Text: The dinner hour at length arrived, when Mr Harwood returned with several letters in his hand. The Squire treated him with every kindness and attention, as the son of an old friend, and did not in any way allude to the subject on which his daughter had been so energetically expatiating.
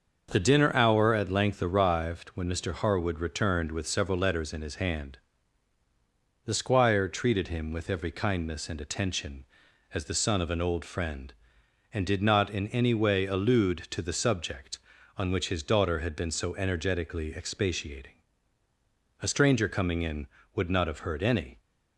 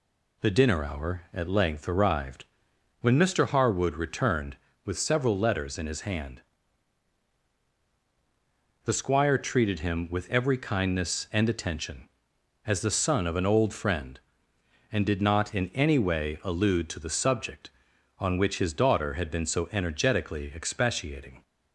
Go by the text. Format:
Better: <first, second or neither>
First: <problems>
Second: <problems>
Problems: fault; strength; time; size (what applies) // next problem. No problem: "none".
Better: second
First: starts louder than the rest; until 1.3 s; 6.5 dB // goes on to say "A stranger coming in would not have heard any"; strong; from 19.2 s on; 2.3 s long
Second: none